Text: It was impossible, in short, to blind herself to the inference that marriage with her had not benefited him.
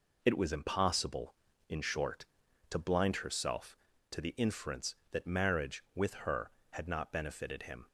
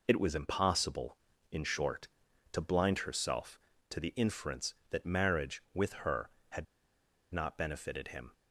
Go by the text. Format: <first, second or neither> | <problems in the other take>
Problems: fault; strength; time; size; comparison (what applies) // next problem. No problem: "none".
first | pauses between "had" and "not"; noticeable; at 6.6 s; 0.67 s long